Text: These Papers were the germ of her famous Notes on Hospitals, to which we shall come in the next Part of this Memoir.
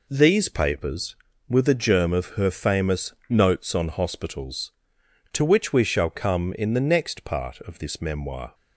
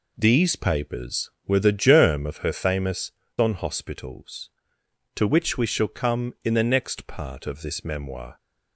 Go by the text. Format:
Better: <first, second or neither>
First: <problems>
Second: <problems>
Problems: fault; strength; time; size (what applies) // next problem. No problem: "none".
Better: first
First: none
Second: skips "Notes"; at 3.2 s